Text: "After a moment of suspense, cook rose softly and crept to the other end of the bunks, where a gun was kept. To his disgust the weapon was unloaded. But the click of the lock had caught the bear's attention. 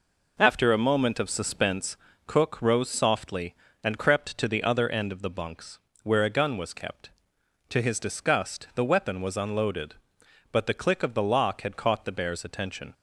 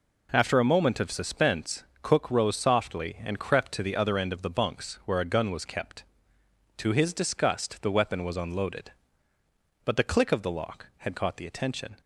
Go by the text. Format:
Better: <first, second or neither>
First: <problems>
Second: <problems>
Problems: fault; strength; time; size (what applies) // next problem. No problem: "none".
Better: first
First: none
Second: skips "bear's"; at 11.4 s